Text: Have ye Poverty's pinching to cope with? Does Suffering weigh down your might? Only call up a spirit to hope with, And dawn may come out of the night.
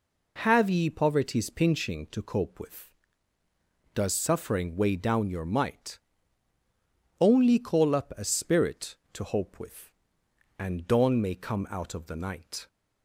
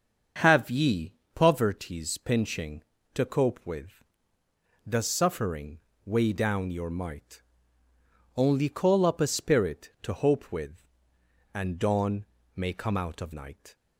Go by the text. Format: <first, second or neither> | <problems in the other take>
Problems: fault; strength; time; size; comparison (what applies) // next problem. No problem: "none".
first | starts louder than the rest; until 1.6 s; 6.5 dB // pauses between "ye" and "Poverty's"; slight; at 1.1 s; 0.20 s long // pauses between "Suffering" and "weigh"; slight; at 5.7 s; 0.26 s long // pauses between "dawn" and "may"; slight; at 12.2 s; 0.28 s long // skips "the"; at 13.3 s